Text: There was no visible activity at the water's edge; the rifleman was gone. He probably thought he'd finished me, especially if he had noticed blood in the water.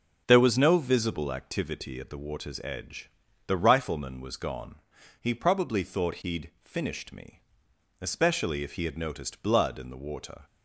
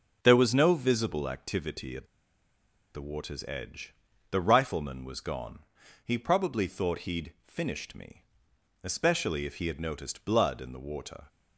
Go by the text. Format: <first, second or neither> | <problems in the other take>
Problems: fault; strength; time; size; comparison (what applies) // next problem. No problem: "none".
first | pauses between "at" and "the"; noticeable; at 2.0 s; 0.89 s long